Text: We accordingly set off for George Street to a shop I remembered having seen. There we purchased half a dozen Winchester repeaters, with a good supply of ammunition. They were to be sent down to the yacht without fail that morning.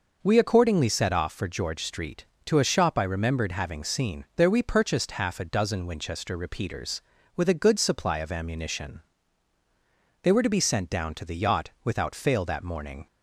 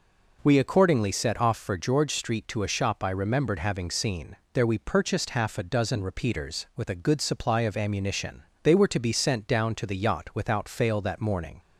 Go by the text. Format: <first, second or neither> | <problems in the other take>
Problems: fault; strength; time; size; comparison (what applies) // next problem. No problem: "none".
first | skips "Winchester"; at 6.0 s